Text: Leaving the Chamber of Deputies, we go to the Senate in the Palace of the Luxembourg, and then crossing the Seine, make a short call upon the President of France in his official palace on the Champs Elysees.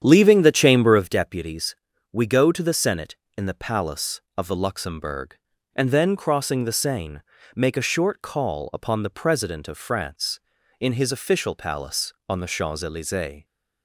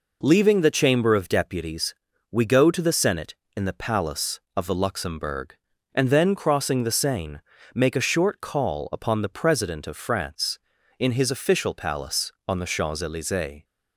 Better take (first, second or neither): second